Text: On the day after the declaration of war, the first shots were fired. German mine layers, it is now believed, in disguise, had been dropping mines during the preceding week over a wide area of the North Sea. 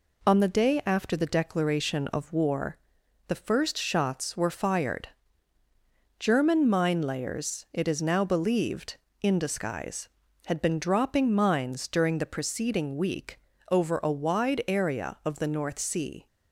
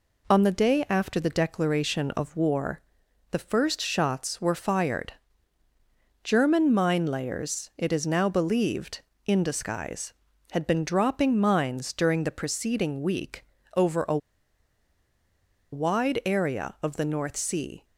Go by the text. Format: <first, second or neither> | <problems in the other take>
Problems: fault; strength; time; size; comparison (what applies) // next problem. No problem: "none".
first | pauses between "week" and "over"; slight; at 13.4 s; 0.30 s long; slight in the first // pauses between "a" and "wide"; strong; at 14.1 s; 1.5 s long